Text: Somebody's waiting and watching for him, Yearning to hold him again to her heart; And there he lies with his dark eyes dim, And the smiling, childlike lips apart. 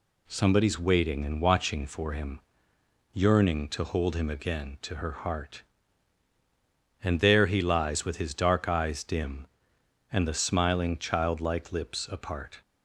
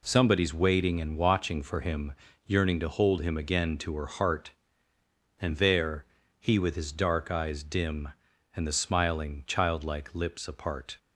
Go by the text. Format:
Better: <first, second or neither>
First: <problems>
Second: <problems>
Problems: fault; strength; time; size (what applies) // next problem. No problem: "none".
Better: first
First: none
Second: pauses between "there" and "he"; slight; at 6.0 s; 0.34 s long // skips "lies"; at 6.5 s